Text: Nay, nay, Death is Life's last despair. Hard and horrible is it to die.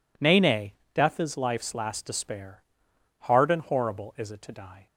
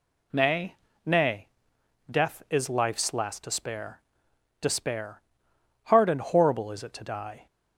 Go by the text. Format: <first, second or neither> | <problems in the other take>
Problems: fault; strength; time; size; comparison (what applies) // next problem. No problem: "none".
first | says "despair" twice; at 4.6 s